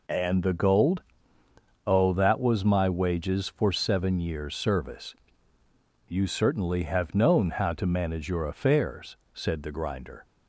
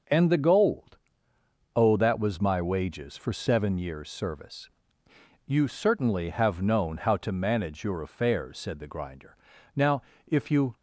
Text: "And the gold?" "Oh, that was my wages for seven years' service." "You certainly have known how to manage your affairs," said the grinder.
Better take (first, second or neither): first